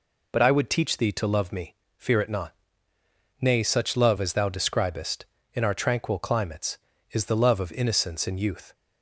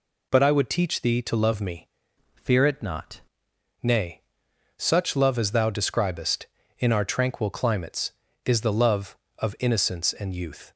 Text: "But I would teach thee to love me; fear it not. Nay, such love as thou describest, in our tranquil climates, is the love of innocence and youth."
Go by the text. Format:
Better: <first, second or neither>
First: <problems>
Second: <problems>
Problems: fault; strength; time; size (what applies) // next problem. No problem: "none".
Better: first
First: none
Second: changes voice from "fear" to "not"; from 2.3 to 3.2 s; 0.9 s long